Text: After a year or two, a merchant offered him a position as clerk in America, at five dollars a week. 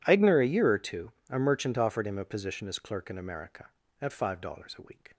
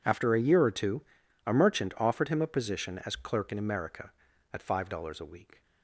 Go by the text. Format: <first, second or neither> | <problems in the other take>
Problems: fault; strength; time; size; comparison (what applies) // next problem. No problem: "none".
second | says "Eigner" for "After"; at 0.0 s